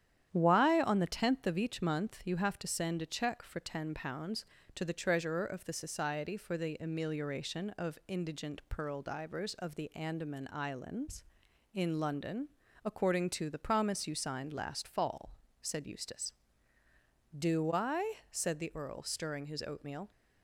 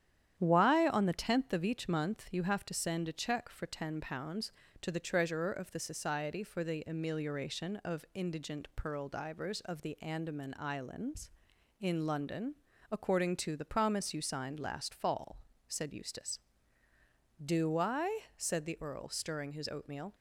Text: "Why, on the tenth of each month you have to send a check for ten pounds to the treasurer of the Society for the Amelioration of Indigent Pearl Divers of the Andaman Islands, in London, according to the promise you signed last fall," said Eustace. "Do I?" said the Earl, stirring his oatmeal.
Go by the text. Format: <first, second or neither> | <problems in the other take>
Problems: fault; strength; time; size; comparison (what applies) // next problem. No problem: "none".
neither | starts louder than the rest; strong; the same in both